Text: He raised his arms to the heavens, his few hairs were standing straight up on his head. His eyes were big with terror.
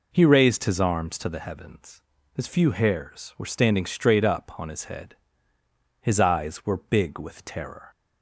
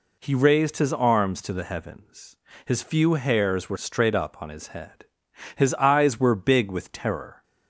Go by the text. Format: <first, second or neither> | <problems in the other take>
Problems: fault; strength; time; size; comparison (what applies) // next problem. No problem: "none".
first | skips "standing"; at 3.7 s